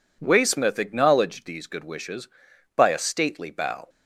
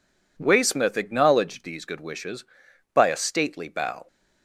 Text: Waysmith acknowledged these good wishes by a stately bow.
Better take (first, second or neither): neither